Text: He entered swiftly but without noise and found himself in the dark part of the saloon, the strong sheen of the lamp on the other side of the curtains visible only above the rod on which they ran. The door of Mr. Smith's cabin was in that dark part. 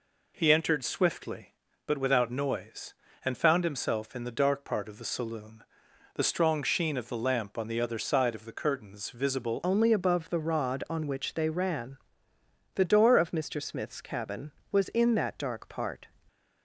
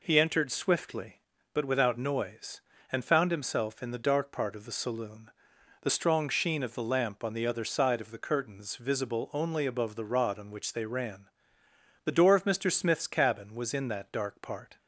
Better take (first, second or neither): second